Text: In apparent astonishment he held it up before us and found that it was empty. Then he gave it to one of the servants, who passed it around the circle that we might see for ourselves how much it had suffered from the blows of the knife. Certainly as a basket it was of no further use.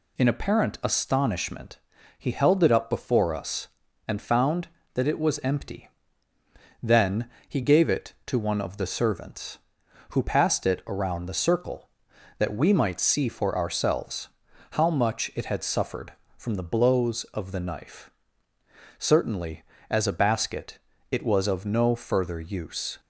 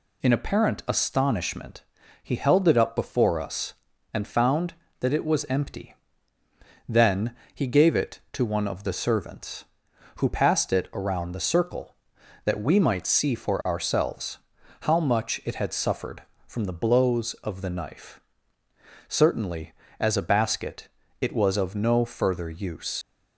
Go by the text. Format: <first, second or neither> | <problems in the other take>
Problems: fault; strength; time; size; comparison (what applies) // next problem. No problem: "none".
first | pauses between "astonishment" and "he"; at 1.8 s; 0.40 s long; also in the first // pauses between "Then" and "he"; slight; at 7.3 s; 0.20 s long; slight in the first // pauses between "ourselves" and "how"; at 14.3 s; 0.44 s long; also in the first // pauses between "basket" and "it"; slight; at 20.8 s; 0.32 s long; slight in the first // leaves "use" unfinished; at 23.0 s; 80 ms